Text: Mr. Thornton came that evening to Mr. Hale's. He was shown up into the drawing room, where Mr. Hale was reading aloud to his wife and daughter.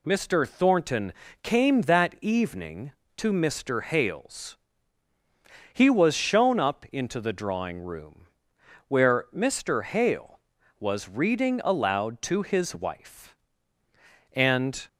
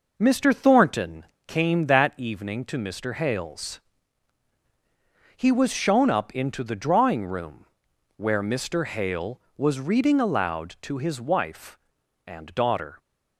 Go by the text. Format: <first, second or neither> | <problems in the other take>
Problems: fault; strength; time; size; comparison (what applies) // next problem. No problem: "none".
second | pauses between "Thornton" and "came"; slight; at 1.1 s; 0.30 s long; slight in the second // stops before "daughter"; at 14.8 s